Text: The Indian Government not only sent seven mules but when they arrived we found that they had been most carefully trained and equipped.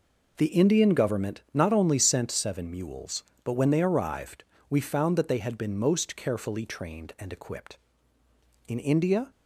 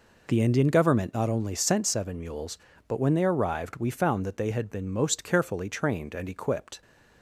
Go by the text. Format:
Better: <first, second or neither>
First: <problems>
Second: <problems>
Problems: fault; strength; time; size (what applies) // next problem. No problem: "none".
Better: second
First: pauses between "arrived" and "we"; slight; at 4.4 s; 0.24 s long // goes on to say "In India"; from 8.6 s on; 0.60 s long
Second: none